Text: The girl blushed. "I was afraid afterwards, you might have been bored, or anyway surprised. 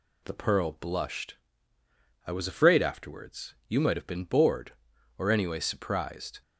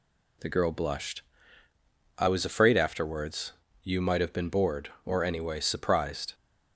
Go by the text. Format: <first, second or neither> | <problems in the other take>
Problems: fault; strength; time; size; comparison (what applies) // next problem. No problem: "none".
second | says "pearl" for "girl"; at 0.3 s